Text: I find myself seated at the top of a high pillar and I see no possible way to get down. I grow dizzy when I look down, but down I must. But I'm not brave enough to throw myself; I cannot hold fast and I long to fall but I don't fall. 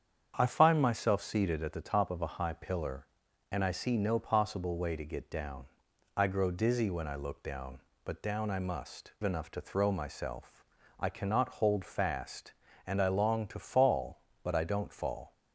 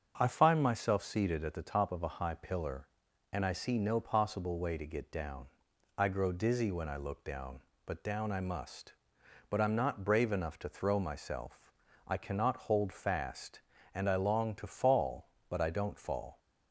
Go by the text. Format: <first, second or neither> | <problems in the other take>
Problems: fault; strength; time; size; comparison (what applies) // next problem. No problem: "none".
second | starts louder than the rest; strong; until 1.3 s; 8 dB; also in the second // skips "But I'm not brave"; at 9.1 s